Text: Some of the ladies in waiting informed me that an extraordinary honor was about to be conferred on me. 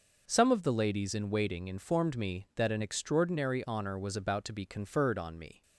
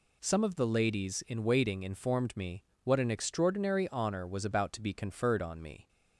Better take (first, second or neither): first